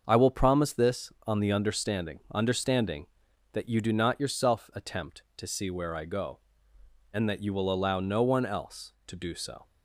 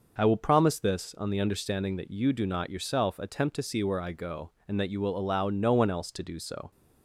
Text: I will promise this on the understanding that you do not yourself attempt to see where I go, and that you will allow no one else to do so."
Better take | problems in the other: second | starts louder than the rest; until 1.0 s; 6.5 dB // says "understanding" twice; at 2.3 s

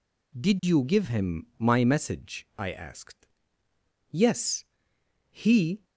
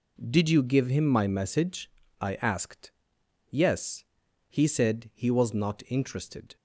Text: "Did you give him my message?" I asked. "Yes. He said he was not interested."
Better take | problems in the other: second | stops before "said he was not interested"; at 5.8 s

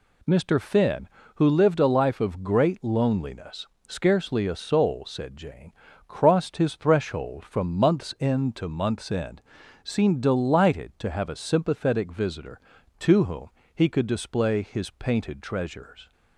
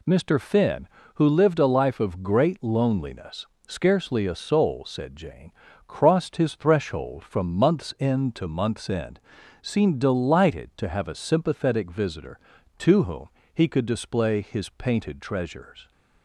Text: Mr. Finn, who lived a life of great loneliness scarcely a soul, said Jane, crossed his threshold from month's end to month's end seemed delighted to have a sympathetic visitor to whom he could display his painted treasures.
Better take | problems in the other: neither | pauses between "loneliness" and "scarcely"; slight; the same in both // pauses between "end" and "seemed"; the same in both // pauses between "whom" and "he"; slight; the same in both

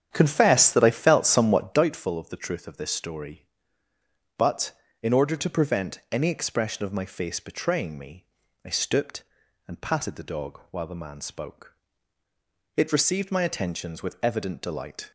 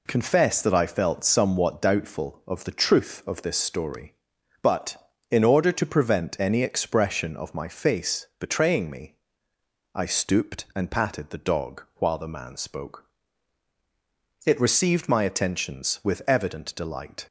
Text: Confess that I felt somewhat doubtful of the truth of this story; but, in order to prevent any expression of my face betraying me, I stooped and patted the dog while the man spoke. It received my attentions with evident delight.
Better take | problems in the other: second | starts louder than the rest; strong; until 2.0 s; 9 dB

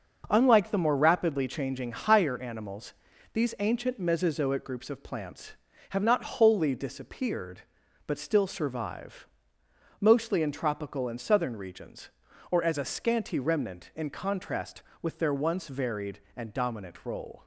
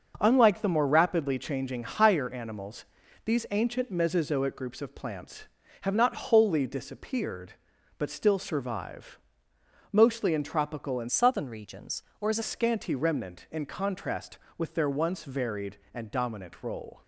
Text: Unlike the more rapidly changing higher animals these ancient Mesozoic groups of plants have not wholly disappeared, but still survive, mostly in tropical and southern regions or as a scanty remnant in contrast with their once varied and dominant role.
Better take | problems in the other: first | starts louder than the rest; until 1.2 s; 6.5 dB; also in the first // pauses between "animals" and "these"; at 2.8 s; 0.40 s long; also in the first // changes voice from "southern" to "a"; from 11.0 to 12.4 s; 1.4 s long

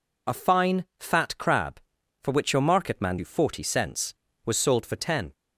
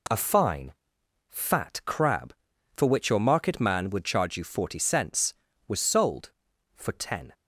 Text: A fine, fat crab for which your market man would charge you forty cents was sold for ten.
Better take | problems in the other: second | skips "would charge"; at 3.1 s

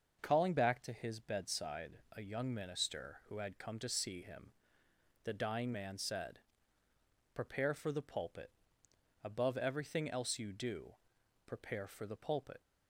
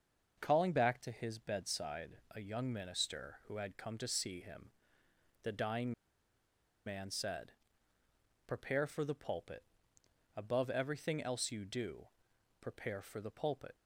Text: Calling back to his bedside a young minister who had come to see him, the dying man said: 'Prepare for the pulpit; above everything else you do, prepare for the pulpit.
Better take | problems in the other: first | starts louder than the rest; until 1.4 s; 6.5 dB; also in the first // pauses between "bedside" and "a"; slight; at 2.1 s; 0.16 s long; slight in the first // pauses between "dying" and "man"; noticeable; at 5.9 s; 0.94 s long

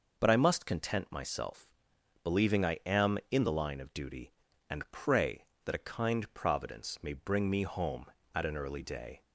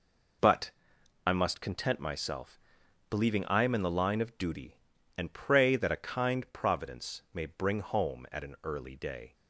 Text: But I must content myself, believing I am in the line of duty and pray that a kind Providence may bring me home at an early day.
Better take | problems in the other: first | pauses between "But" and "I"; noticeable; at 0.7 s; 0.56 s long // skips "me"; at 7.8 s

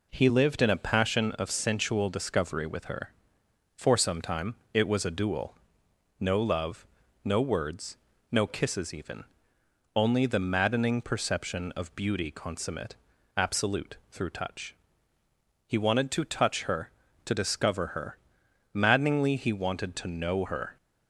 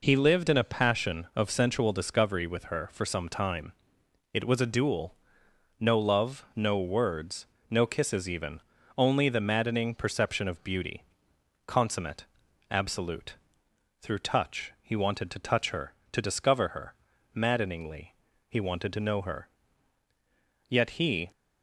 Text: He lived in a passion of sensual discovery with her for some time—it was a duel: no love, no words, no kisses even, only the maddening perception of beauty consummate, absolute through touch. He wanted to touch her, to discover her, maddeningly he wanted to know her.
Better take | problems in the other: first | pauses between "beauty" and "consummate"; noticeable; at 11.0 s; 0.64 s long // pauses between "absolute" and "through"; noticeable; at 13.3 s; 0.64 s long; slight in the first // pauses between "maddeningly" and "he"; slight; at 18.1 s; 0.34 s long // goes on to say "Yet he"; noticeable; from 20.6 s on; 0.62 s long

